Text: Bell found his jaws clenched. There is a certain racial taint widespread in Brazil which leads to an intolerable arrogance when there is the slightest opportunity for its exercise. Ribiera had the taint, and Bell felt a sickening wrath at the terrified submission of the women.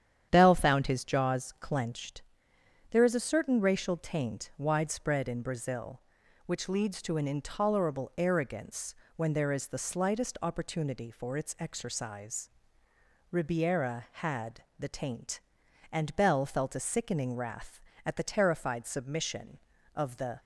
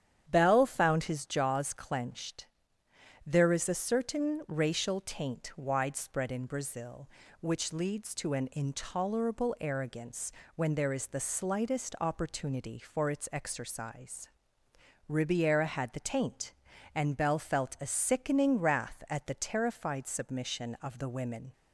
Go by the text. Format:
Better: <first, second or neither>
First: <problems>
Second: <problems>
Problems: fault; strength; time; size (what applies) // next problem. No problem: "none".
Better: second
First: starts louder than the rest; strong; until 1.3 s; 9.5 dB // pauses between "arrogance" and "when"; slight; at 8.9 s; 0.20 s long // stops before "women"; at 20.3 s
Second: starts louder than the rest; strong; until 1.2 s; 9.5 dB // pauses between "arrogance" and "when"; slight; at 10.3 s; 0.24 s long